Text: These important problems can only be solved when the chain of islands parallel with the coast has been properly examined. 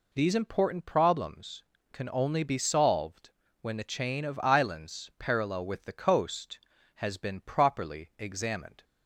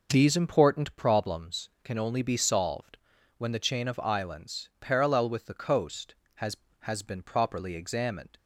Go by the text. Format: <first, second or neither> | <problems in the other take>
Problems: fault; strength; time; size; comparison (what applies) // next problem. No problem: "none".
first | pauses between "solved" and "when"; at 2.9 s; 0.40 s long; slight in the first // says "has" twice; at 6.8 s